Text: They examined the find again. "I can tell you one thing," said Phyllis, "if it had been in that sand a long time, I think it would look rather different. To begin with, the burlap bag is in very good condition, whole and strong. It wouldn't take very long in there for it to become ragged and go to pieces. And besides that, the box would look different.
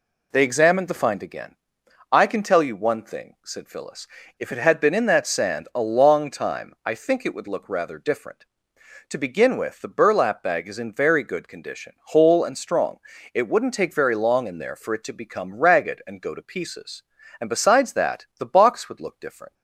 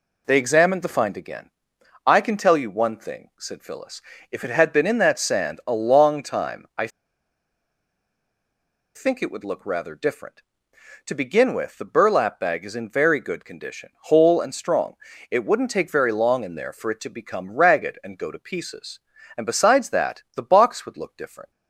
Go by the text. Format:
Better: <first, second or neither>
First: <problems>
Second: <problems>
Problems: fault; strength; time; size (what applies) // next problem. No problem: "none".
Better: first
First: none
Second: pauses between "I" and "think"; strong; at 6.8 s; 2.0 s long